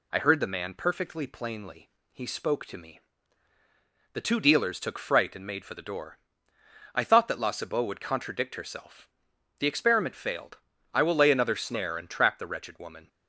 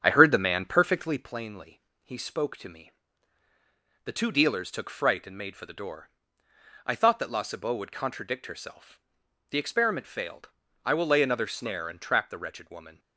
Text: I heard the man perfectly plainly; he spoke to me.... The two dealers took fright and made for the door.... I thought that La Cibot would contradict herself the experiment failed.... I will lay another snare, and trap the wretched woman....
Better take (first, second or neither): first